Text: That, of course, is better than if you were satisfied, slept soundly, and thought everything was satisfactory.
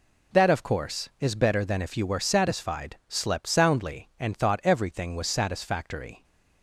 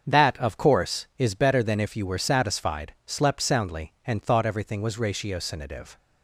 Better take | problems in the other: first | starts louder than the rest; strong; until 1.1 s; 7.5 dB // says "ratiocinative" for "satisfactory"; at 4.9 s

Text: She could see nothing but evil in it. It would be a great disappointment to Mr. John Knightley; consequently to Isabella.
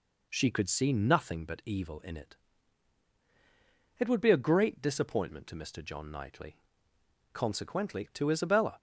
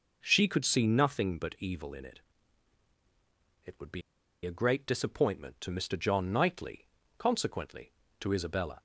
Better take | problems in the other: first | pauses between "be" and "a"; at 4.0 s; 0.44 s long

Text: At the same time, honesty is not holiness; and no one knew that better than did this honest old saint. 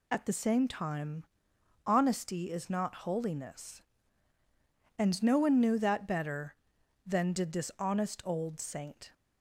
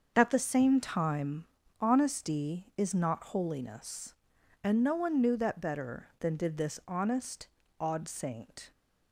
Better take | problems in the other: first | starts louder than the rest; until 1.1 s; 6.5 dB // says "odd" for "old"; at 7.7 s

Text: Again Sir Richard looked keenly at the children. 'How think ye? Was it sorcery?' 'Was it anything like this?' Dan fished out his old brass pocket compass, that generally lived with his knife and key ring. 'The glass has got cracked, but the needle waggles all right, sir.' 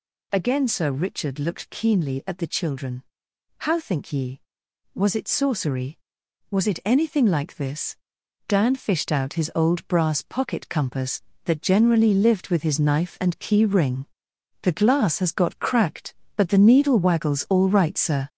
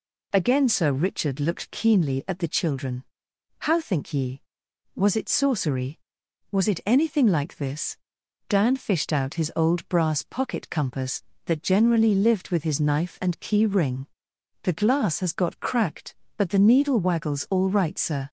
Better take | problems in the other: second | gets louder; noticeable; throughout; 4.5 dB

